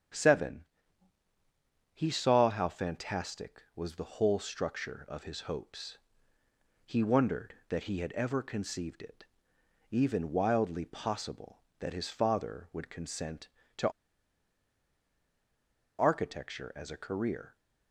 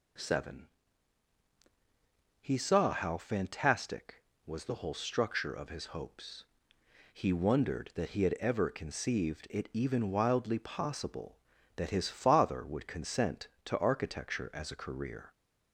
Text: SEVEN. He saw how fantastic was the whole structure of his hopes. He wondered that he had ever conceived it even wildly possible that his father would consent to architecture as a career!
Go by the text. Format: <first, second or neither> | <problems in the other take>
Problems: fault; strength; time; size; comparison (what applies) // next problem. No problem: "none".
second | starts louder than the rest; strong; until 2.4 s; 8.5 dB // pauses between "it" and "even"; noticeable; at 9.2 s; 0.66 s long // pauses between "to" and "architecture"; strong; at 13.8 s; 2.1 s long